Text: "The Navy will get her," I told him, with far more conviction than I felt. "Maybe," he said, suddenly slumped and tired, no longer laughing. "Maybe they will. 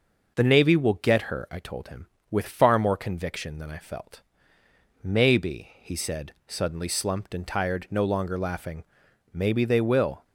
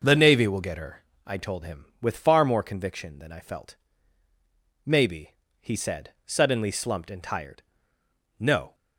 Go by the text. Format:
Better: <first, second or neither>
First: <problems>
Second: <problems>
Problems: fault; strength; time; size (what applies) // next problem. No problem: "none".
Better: first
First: none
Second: starts louder than the rest; noticeable; until 1.0 s; 6 dB // stops before "longer laughing Maybe they will"; at 8.7 s